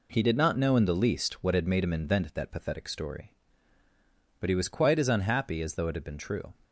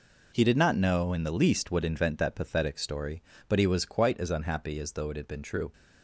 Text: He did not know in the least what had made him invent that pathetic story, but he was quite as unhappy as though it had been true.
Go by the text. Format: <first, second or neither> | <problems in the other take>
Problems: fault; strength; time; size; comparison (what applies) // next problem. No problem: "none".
first | skips "had made him"; at 1.8 s